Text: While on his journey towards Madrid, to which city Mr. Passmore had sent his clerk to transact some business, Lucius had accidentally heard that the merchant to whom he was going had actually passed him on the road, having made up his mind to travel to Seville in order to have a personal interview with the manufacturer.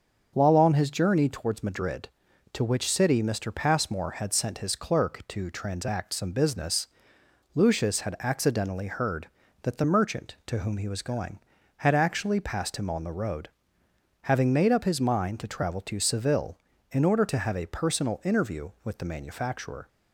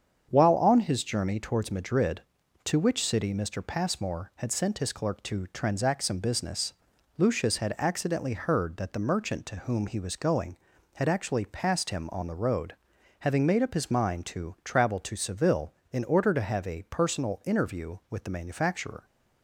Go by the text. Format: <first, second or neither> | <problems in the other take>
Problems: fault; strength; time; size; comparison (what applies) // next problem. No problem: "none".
neither | starts louder than the rest; the same in both